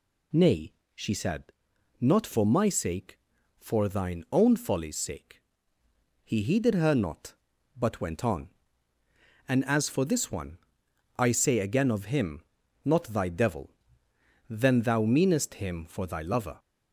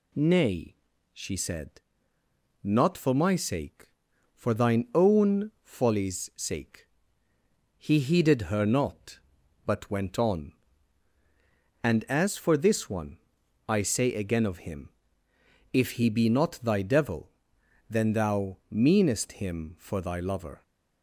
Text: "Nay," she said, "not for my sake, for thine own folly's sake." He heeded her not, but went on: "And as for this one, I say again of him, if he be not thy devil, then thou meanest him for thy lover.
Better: second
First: skips "if he be"; at 12.6 s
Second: none

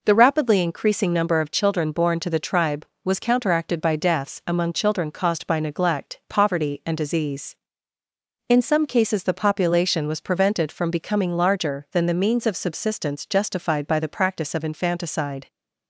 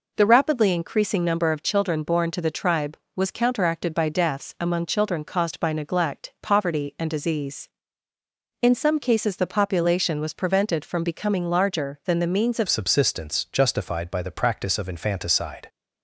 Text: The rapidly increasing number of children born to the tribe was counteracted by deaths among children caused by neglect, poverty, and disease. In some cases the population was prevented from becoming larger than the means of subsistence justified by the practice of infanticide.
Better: first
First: none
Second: changes voice at "subsistence"; from 12.6 s on; 3.0 s long

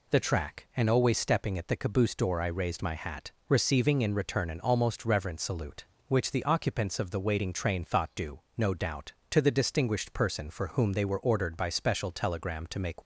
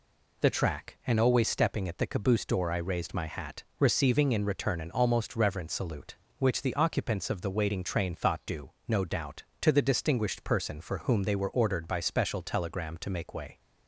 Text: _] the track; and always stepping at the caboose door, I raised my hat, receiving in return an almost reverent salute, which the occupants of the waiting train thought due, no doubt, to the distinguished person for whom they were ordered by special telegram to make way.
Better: second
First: stops before "way"; at 13.0 s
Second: none

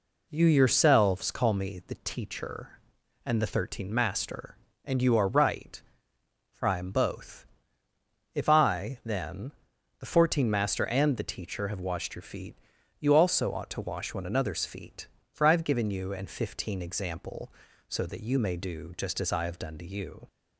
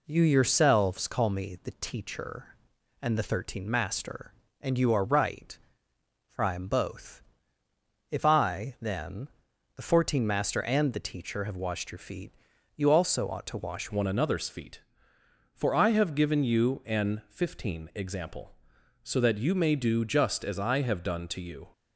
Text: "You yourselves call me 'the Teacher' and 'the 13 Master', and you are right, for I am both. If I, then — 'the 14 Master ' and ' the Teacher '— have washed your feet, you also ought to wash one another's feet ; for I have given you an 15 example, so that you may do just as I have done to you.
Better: first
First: none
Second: changes voice at "one"; from 13.8 s on; 7.8 s long

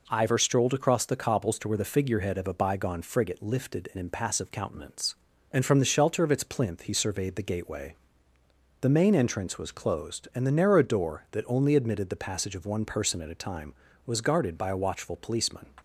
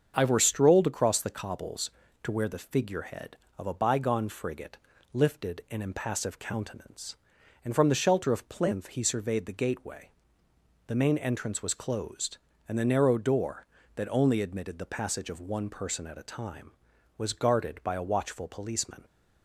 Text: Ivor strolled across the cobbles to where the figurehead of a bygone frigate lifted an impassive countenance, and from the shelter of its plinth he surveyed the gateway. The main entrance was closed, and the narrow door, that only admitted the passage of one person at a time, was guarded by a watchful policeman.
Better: first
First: none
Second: starts louder than the rest; until 1.1 s; 7 dB // pauses between "frigate" and "lifted"; slight; at 4.7 s; 0.36 s long // skips "its"; at 8.4 s

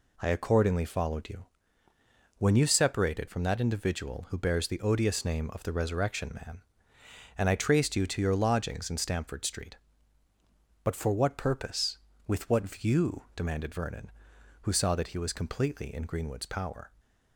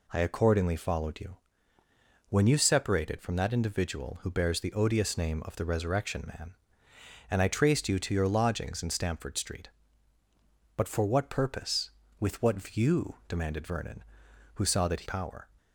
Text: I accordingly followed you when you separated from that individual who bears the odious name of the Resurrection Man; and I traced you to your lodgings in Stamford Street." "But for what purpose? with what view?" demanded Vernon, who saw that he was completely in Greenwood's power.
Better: first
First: pauses between "you" and "when"; noticeable; at 1.4 s; 0.94 s long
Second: pauses between "you" and "when"; noticeable; at 1.3 s; 0.94 s long // skips "was completely in Greenwood's"; at 15.0 s

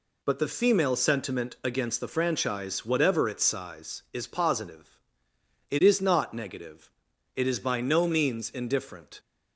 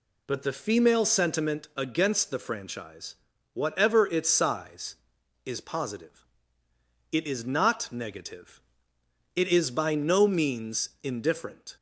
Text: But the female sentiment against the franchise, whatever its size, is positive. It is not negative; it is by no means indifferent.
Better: neither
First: none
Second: none

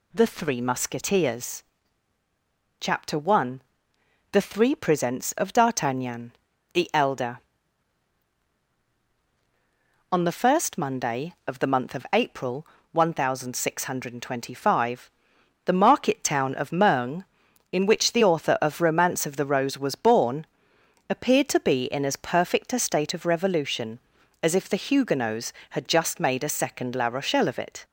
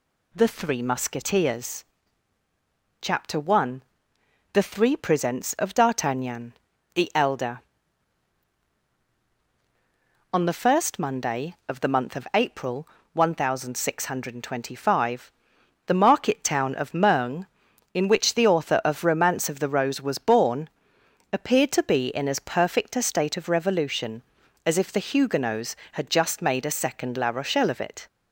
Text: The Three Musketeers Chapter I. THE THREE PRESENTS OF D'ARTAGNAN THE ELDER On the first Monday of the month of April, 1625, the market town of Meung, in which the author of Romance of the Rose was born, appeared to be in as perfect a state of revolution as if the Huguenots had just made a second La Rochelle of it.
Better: neither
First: pauses between "Musketeers" and "Chapter"; at 1.6 s; 1.1 s long // pauses between "D'ARTAGNAN" and "THE"; at 6.3 s; 0.40 s long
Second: pauses between "Musketeers" and "Chapter"; at 1.8 s; 1.1 s long // pauses between "D'ARTAGNAN" and "THE"; at 6.5 s; 0.40 s long

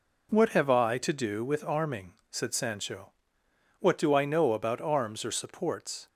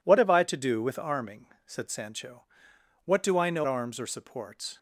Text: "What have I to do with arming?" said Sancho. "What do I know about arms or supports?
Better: first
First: none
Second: skips "about"; at 3.6 s

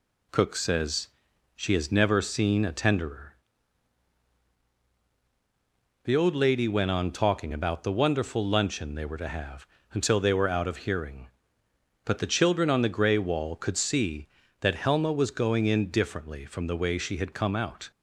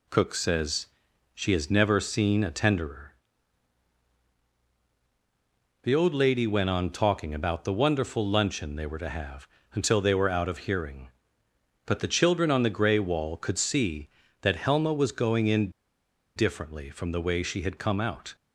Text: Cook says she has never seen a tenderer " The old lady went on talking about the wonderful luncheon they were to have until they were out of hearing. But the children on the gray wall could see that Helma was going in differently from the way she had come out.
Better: first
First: pauses between "says" and "she"; noticeable; at 1.0 s; 0.48 s long // pauses between "have" and "until"; slight; at 9.6 s; 0.26 s long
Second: pauses between "says" and "she"; noticeable; at 0.8 s; 0.48 s long // pauses between "have" and "until"; slight; at 9.4 s; 0.26 s long // pauses between "in" and "differently"; noticeable; at 15.7 s; 0.64 s long

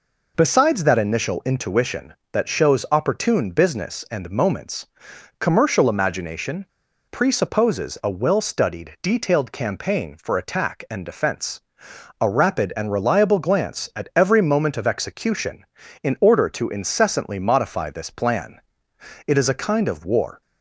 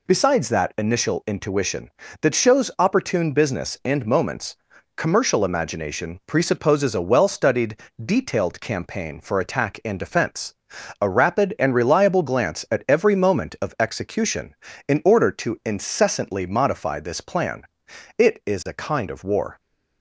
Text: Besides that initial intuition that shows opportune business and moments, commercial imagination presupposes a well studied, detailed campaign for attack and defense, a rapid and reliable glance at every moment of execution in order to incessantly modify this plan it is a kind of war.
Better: second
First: pauses between "imagination" and "presupposes"; at 6.6 s; 0.45 s long // pauses between "plan" and "it"; noticeable; at 18.5 s; 0.68 s long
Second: pauses between "plan" and "it"; noticeable; at 17.6 s; 0.54 s long

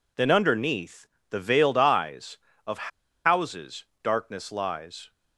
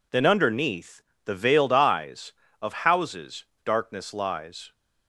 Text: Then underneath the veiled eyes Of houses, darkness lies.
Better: second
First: pauses between "underneath" and "the"; slight; at 1.0 s; 0.24 s long // pauses between "Of" and "houses"; slight; at 2.8 s; 0.35 s long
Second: pauses between "underneath" and "the"; slight; at 1.0 s; 0.24 s long

